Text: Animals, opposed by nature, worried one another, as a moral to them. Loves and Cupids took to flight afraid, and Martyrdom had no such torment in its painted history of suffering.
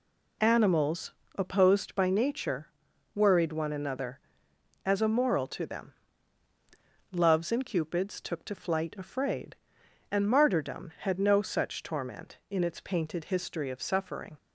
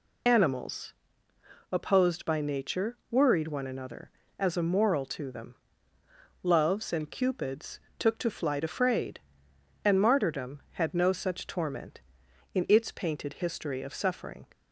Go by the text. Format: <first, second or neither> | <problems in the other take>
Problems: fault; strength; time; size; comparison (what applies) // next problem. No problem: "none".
first | loses the start of "Animals"; at 0.2 s; 40 ms // pauses between "Cupids" and "took"; slight; at 7.7 s; 0.22 s long